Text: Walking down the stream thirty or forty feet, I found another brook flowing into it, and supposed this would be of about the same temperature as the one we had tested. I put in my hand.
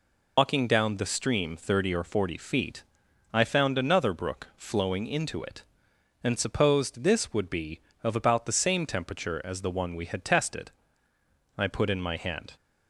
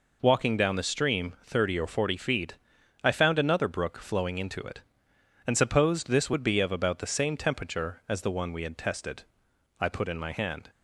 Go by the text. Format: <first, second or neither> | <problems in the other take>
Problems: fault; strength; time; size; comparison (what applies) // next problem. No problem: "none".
second | loses the start of "Walking"; at 0.3 s; 100 ms